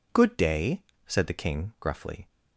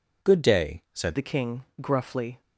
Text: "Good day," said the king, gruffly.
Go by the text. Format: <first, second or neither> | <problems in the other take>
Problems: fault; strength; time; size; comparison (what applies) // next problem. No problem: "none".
first | changes voice at "the"; from 1.1 s on; 1.3 s long